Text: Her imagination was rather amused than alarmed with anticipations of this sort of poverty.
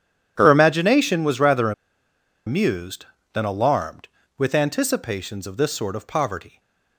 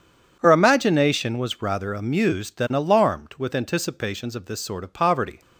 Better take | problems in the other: second | pauses between "rather" and "amused"; noticeable; at 1.7 s; 0.75 s long

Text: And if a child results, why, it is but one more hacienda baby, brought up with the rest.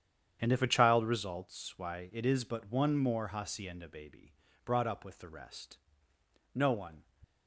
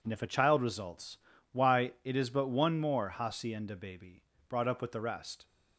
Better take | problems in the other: second | starts louder than the rest; strong; until 1.4 s; 9 dB // goes on to say "No one"; slight; from 6.5 s on; 0.48 s long

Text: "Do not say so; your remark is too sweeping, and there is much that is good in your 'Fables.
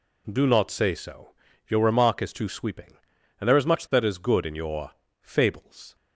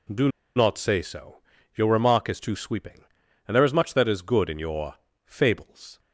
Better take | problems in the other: first | pauses between "Do" and "not"; slight; at 0.2 s; 0.28 s long // pauses between "your" and "Fables"; slight; at 4.9 s; 0.30 s long; slight in the first

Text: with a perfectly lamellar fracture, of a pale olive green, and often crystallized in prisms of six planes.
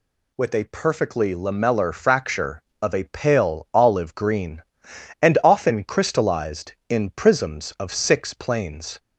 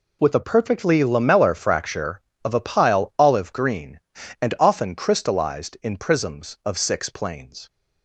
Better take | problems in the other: first | says "pile" for "pale"; at 2.5 s

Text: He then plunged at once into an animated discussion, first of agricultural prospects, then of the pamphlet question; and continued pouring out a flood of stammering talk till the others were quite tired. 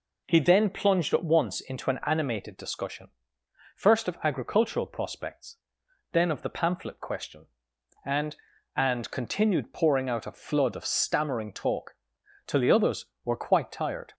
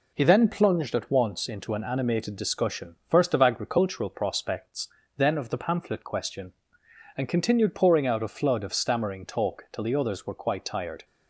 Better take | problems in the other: second | says "and" twice; at 8.7 s // pauses between "talk" and "till"; noticeable; at 11.9 s; 0.50 s long

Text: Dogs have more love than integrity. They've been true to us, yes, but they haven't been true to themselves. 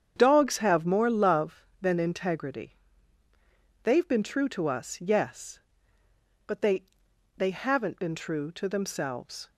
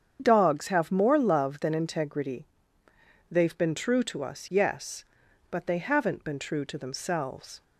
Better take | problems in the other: second | starts louder than the rest; strong; until 1.1 s; 8 dB; strong in the second // says "they" twice; at 7.3 s

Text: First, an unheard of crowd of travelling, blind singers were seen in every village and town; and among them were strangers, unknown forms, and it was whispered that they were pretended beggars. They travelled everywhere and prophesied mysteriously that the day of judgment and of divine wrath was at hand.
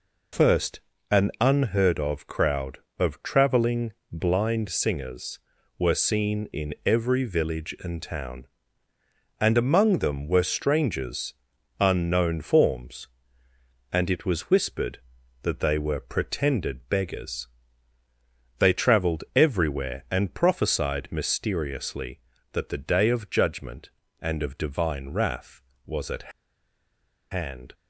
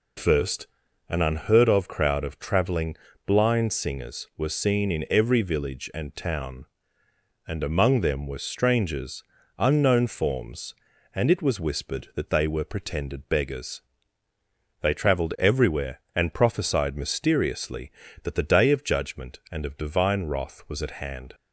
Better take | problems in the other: second | pauses between "at" and "hand"; at 26.3 s; 1.0 s long

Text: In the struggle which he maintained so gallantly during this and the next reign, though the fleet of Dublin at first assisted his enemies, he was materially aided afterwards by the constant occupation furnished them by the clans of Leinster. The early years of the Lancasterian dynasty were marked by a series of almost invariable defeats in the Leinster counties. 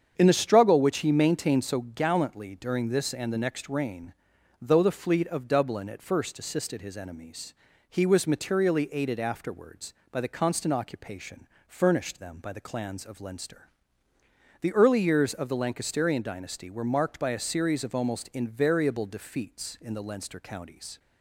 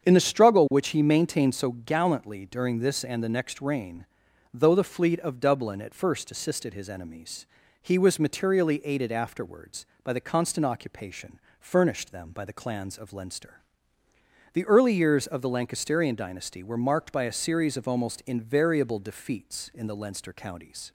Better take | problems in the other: neither | starts louder than the rest; strong; the same in both // pauses between "occupation" and "furnished"; slight; the same in both

